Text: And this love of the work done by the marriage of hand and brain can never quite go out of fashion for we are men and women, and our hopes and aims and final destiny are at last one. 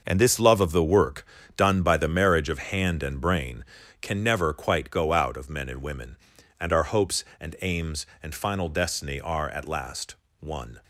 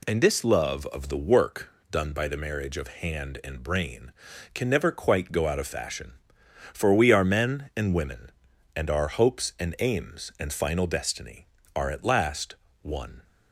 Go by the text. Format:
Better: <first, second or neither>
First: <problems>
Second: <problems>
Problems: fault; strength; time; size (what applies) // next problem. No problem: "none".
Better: second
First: starts louder than the rest; noticeable; until 1.0 s; 6 dB // pauses between "work" and "done"; slight; at 1.2 s; 0.30 s long // skips "fashion for we are"; at 5.4 s // pauses between "last" and "one"; slight; at 10.1 s; 0.26 s long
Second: pauses between "work" and "done"; slight; at 1.6 s; 0.20 s long // pauses between "last" and "one"; slight; at 12.5 s; 0.26 s long